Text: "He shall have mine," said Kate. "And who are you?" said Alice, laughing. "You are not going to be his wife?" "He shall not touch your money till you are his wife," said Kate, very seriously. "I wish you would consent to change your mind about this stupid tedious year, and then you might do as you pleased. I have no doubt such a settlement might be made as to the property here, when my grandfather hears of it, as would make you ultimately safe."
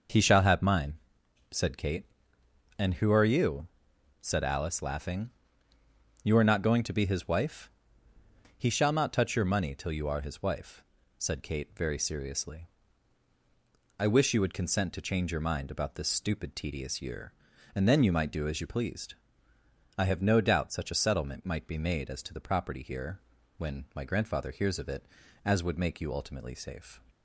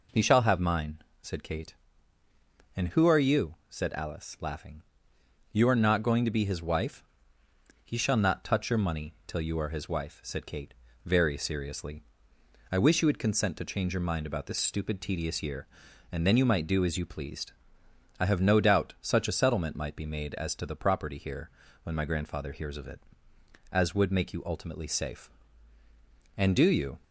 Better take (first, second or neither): first